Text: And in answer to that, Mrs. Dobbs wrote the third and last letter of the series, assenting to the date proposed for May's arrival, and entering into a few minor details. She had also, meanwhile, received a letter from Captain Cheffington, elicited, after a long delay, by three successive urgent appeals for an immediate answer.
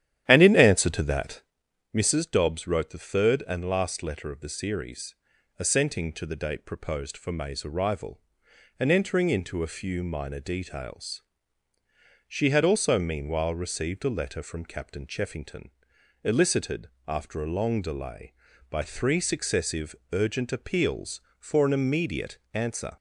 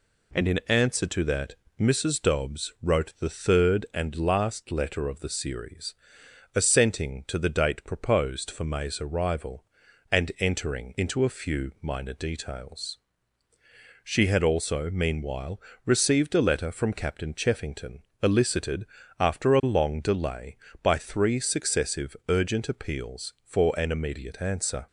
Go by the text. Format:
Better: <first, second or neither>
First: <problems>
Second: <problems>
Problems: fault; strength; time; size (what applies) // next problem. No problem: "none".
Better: second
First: starts louder than the rest; strong; until 1.6 s; 11.5 dB // pauses between "successive" and "urgent"; slight; at 19.9 s; 0.18 s long // pauses between "immediate" and "answer"; slight; at 22.3 s; 0.16 s long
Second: none